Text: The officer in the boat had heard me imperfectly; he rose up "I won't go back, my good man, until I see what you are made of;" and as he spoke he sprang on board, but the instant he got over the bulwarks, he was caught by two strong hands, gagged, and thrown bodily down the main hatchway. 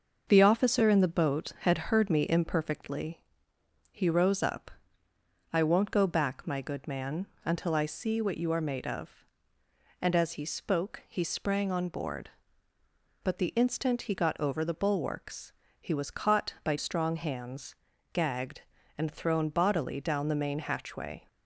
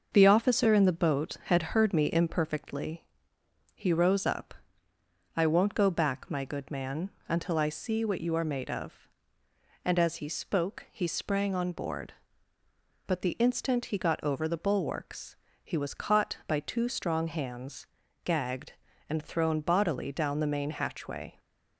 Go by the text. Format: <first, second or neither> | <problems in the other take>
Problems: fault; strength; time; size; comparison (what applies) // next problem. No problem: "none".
second | pauses between "up" and "I"; noticeable; at 4.6 s; 0.84 s long; noticeable in the second // skips "two"; at 16.7 s